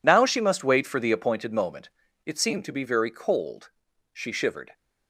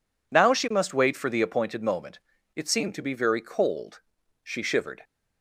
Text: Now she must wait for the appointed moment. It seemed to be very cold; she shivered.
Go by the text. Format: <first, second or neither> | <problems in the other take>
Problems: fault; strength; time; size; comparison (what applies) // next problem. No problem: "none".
second | gets quieter; strong; throughout; 14.5 dB